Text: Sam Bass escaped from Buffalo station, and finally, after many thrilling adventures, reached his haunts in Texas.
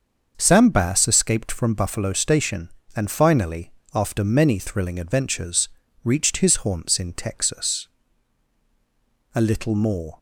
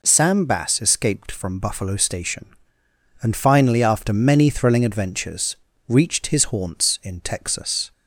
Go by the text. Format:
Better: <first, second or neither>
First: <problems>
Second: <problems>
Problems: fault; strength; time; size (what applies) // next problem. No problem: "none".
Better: second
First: starts louder than the rest; until 1.3 s; 6.5 dB // goes on to say "A little more"; noticeable; from 9.3 s on; 0.84 s long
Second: none